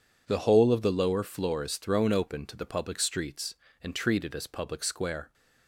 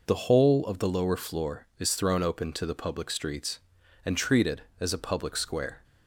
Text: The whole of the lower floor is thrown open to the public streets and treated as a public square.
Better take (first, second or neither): second